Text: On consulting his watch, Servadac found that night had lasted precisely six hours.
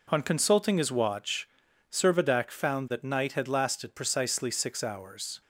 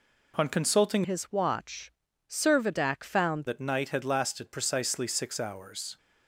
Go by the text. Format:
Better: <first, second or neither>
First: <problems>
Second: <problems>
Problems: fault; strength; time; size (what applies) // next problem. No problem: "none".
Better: first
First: none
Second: changes voice from "his" to "found"; from 1.0 to 3.4 s; 2.4 s long